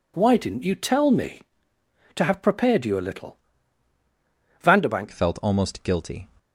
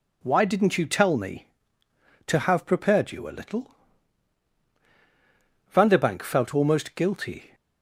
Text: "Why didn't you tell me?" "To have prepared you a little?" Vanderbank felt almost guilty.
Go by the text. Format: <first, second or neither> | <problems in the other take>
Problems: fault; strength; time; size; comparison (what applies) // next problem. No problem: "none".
second | changes voice at "felt"; from 5.1 s on; 1.1 s long